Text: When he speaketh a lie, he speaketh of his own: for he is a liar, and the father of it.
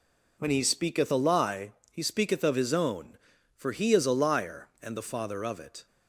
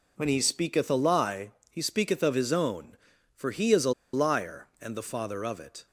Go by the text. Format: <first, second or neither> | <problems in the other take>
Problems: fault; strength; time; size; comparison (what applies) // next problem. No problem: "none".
first | pauses between "a" and "liar"; slight; at 3.9 s; 0.22 s long